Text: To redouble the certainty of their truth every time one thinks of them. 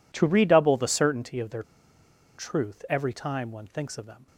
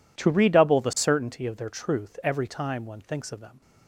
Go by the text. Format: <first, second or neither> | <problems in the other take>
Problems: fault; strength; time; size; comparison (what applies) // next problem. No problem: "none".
second | pauses between "their" and "truth"; noticeable; at 1.6 s; 0.75 s long